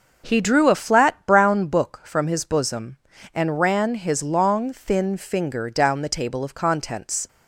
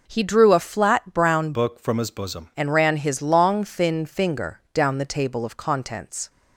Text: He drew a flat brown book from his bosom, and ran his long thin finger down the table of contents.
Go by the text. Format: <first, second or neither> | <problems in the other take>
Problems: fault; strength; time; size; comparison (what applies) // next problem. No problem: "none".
first | changes voice from "book" to "bosom"; from 1.5 to 2.4 s; 0.9 s long